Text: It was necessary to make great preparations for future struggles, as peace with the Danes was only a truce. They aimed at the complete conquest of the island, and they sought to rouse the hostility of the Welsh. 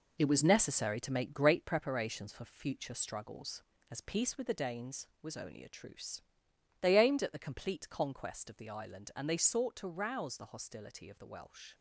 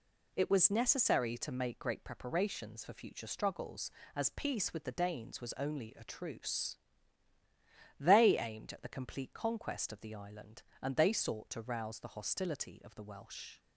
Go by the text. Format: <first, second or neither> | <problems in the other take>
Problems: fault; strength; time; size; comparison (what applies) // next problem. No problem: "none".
second | gets quieter; strong; throughout; 7.5 dB